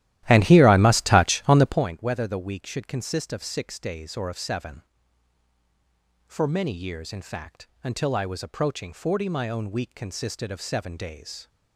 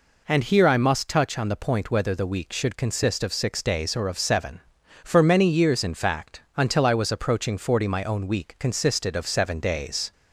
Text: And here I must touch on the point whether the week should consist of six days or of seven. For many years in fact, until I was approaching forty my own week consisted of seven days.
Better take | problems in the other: second | starts louder than the rest; strong; until 1.8 s; 14 dB

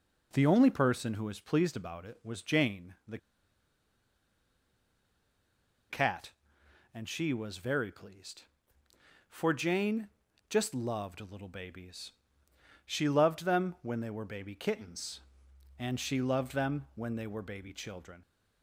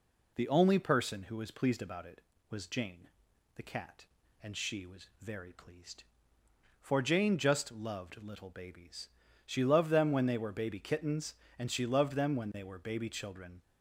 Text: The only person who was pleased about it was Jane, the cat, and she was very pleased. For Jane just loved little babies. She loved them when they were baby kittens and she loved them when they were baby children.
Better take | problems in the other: second | pauses between "the" and "cat"; strong; at 3.1 s; 2.7 s long // pauses between "Jane" and "just"; at 10.0 s; 0.42 s long

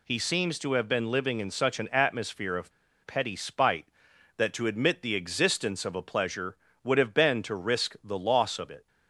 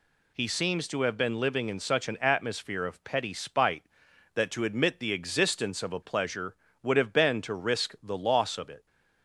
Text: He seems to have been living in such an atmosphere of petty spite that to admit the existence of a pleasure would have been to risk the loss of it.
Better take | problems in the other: second | pauses between "of" and "petty"; slight; at 2.7 s; 0.34 s long

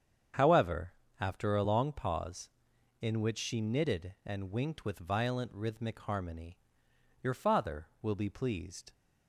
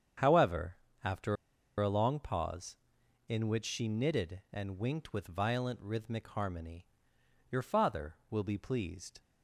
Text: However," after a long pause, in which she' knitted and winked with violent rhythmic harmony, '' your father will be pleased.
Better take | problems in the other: first | starts louder than the rest; strong; until 1.9 s; 8 dB; strong in the first // pauses between "after" and "a"; at 1.3 s; 0.44 s long

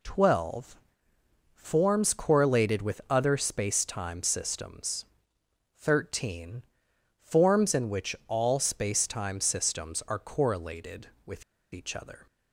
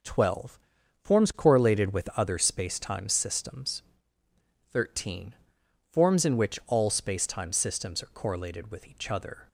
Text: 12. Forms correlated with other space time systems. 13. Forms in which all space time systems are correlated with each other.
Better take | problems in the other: second | pauses between "with" and "each"; slight; at 11.4 s; 0.30 s long

